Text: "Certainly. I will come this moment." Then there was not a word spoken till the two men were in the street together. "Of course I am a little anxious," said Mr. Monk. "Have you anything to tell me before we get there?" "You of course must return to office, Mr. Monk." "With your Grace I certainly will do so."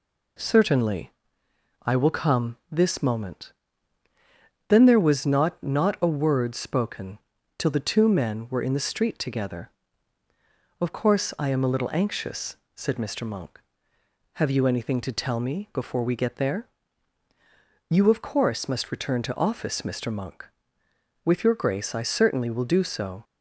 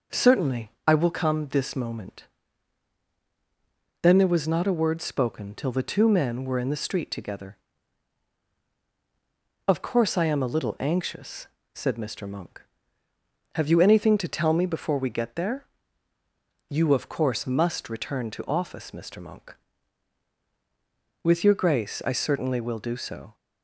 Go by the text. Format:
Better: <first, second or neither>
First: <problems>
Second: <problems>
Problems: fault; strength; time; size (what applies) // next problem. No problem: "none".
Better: second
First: says "not" twice; at 5.6 s // pauses between "spoken" and "till"; at 7.1 s; 0.40 s long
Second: none